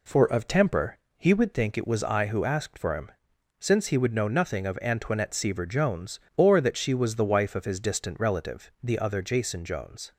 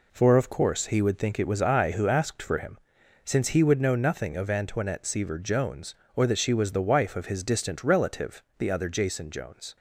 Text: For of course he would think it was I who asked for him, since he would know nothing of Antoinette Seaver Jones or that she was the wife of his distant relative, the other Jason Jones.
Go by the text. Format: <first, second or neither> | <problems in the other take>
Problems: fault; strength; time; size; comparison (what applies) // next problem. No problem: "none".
second | says "temper" for "course"; at 0.4 s